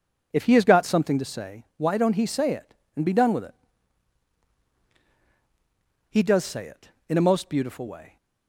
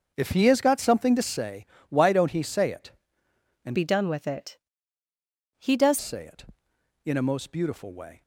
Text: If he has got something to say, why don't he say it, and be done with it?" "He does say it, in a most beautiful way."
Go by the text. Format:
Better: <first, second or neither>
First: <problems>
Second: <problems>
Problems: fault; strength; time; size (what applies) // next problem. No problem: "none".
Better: first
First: none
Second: starts louder than the rest; until 1.1 s; 6.5 dB // changes voice from "be" to "does"; from 3.7 to 5.9 s; 2.2 s long